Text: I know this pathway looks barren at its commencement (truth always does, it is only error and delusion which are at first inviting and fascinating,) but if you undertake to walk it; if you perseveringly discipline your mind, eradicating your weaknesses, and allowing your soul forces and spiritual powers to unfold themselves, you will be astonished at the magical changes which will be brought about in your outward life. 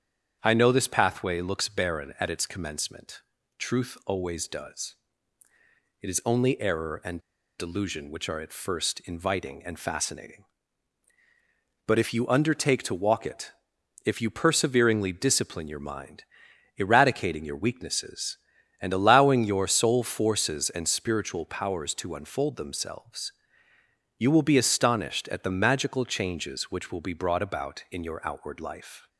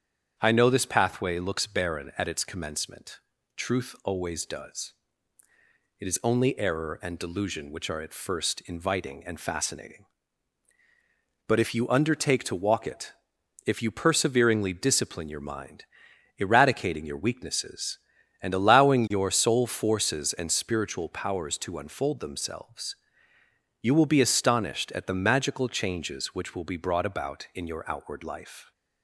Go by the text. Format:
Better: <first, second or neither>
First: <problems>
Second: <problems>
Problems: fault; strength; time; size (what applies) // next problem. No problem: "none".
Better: second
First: starts louder than the rest; strong; until 1.4 s; 8.5 dB // pauses between "and" and "delusion"; at 7.1 s; 0.39 s long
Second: starts louder than the rest; strong; until 1.3 s; 8.5 dB